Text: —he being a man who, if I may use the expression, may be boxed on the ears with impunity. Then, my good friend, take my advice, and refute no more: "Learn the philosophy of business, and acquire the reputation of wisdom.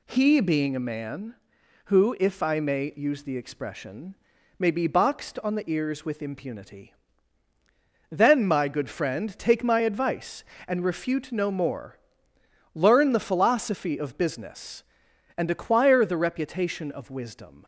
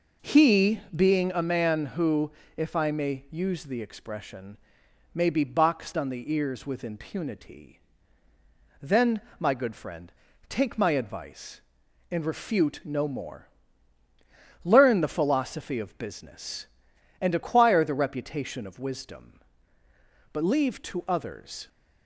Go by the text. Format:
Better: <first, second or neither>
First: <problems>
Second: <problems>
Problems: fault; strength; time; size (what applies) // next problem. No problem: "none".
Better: first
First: none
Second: goes on to say "But leave to others"; from 20.3 s on; 1.3 s long